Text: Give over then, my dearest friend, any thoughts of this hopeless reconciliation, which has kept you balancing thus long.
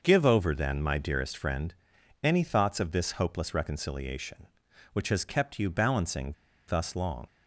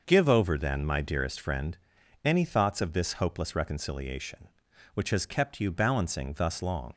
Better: second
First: starts louder than the rest; noticeable; until 1.0 s; 6 dB // pauses between "balancing" and "thus"; slight; at 6.3 s; 0.35 s long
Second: none

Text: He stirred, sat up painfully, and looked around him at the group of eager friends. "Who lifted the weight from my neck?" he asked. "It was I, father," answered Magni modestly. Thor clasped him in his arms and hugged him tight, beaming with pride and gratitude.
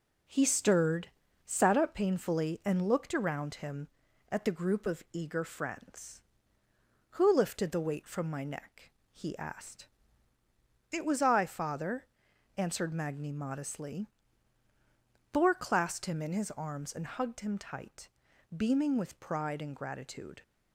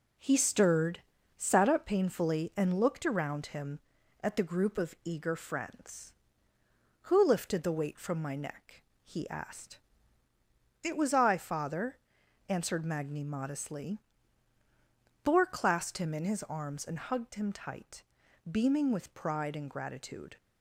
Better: neither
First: none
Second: none

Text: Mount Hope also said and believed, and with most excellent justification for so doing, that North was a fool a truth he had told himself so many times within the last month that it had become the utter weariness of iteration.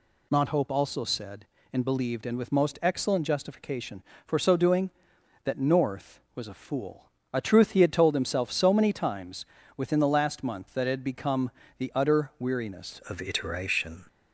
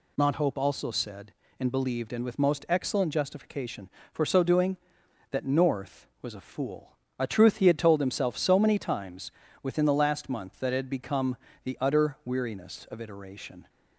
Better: second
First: pauses between "fool" and "a"; slight; at 7.0 s; 0.26 s long // pauses between "times" and "within"; slight; at 9.4 s; 0.32 s long // pauses between "become" and "the"; slight; at 11.5 s; 0.26 s long // changes voice at "of"; from 13.0 s on; 1.0 s long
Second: pauses between "fool" and "a"; slight; at 6.9 s; 0.25 s long // pauses between "times" and "within"; slight; at 9.3 s; 0.32 s long // pauses between "become" and "the"; slight; at 11.3 s; 0.26 s long

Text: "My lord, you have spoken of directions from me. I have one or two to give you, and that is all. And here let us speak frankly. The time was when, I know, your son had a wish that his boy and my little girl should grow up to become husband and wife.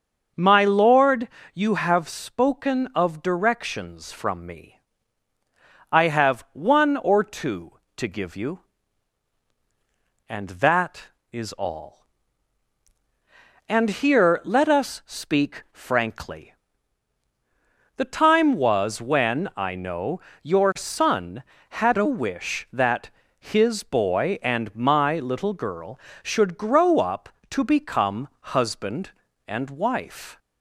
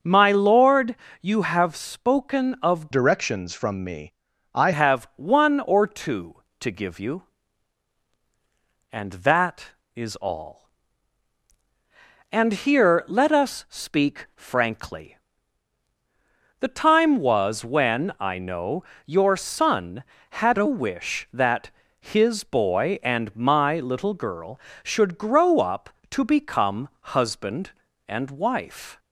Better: first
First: starts louder than the rest; until 1.6 s; 6.5 dB // pauses between "that" and "his"; slight; at 23.0 s; 0.30 s long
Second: starts louder than the rest; until 1.2 s; 6.5 dB // changes voice from "directions" to "I"; from 2.9 to 4.7 s; 1.8 s long // pauses between "that" and "his"; slight; at 21.6 s; 0.30 s long

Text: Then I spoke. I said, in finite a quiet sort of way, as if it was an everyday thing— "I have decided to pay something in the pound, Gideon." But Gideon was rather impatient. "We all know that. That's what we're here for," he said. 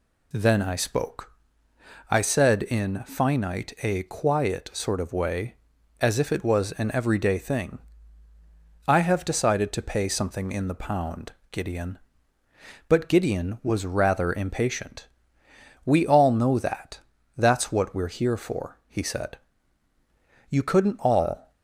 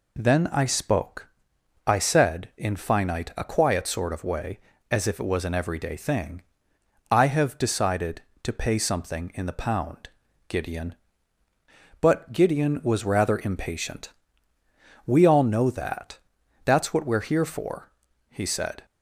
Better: second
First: goes on to say "You couldn't all"; noticeable; from 20.4 s on; 1.0 s long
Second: none

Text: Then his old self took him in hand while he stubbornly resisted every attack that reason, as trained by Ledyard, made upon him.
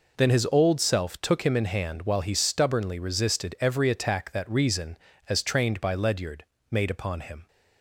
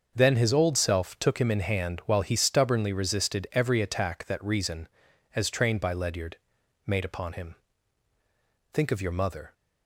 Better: first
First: none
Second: starts louder than the rest; until 1.1 s; 6 dB // goes on to say "Think of your mother"; noticeable; from 8.7 s on; 0.80 s long

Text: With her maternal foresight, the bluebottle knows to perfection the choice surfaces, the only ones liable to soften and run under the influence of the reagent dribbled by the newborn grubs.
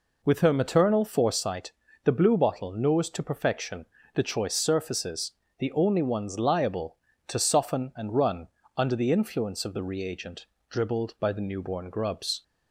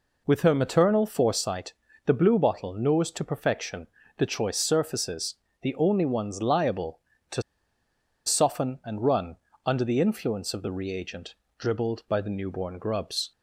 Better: first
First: pauses between "perfection" and "the"; slight; at 3.8 s; 0.26 s long // pauses between "run" and "under"; slight; at 8.4 s; 0.28 s long // pauses between "reagent" and "dribbled"; slight; at 10.4 s; 0.24 s long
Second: pauses between "perfection" and "the"; slight; at 3.8 s; 0.28 s long // pauses between "to" and "soften"; noticeable; at 7.4 s; 0.84 s long // pauses between "run" and "under"; slight; at 9.3 s; 0.28 s long // pauses between "reagent" and "dribbled"; slight; at 11.3 s; 0.24 s long

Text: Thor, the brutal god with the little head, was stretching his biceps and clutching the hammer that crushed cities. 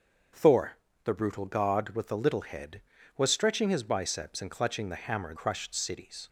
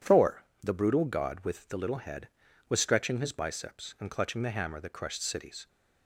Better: second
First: starts louder than the rest; until 1.6 s; 7 dB // skips "that"; at 5.3 s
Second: none

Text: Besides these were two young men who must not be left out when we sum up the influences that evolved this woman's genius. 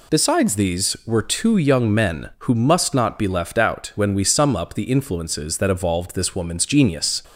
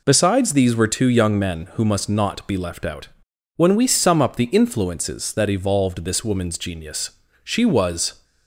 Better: first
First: none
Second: pauses between "out" and "when"; noticeable; at 3.0 s; 0.48 s long // goes on to say "She was"; noticeable; from 7.4 s on; 0.80 s long

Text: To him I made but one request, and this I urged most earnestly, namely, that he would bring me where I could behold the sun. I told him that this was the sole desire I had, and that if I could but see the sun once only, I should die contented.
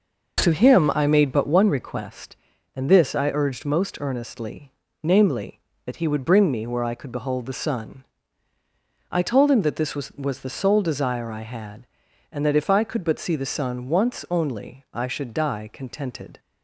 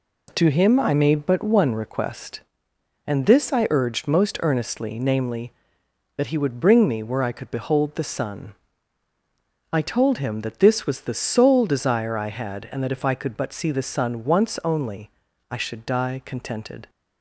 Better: second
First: says "was" twice; at 10.1 s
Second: none

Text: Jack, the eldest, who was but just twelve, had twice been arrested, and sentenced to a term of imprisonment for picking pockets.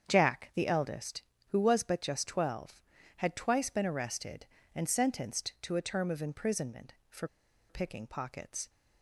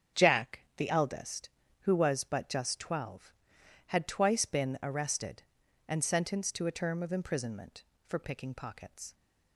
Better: second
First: starts louder than the rest; strong; until 1.0 s; 7.5 dB // pauses between "for" and "picking"; at 7.2 s; 0.42 s long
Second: starts louder than the rest; strong; until 1.3 s; 7.5 dB

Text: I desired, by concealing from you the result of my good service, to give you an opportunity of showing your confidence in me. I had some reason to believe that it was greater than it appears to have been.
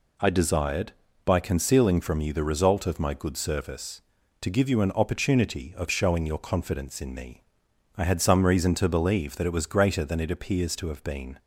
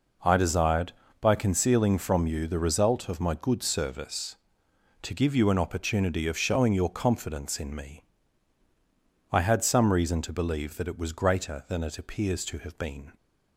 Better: neither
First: none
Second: none

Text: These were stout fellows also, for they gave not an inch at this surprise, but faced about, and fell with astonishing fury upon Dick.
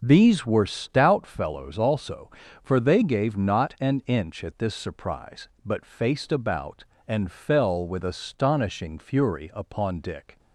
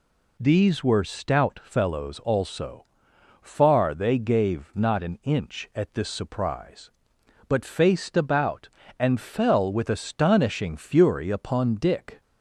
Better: first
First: none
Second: says "far" for "for"; at 3.4 s

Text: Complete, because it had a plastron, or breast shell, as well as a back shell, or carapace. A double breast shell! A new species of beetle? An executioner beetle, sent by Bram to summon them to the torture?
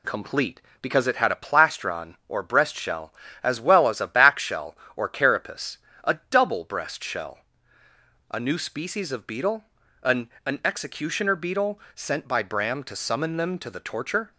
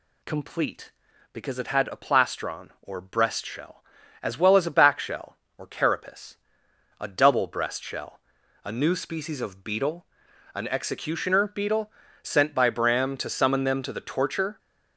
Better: second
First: says "An" twice; at 10.4 s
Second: none

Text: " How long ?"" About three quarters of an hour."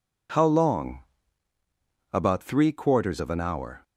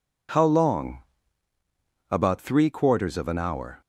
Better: neither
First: none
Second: none

